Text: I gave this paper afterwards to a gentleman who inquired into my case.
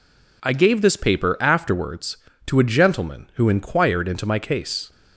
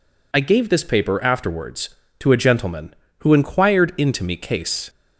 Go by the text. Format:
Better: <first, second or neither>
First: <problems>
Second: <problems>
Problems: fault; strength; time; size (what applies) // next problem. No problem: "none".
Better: first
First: none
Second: says "me" for "my"; at 4.2 s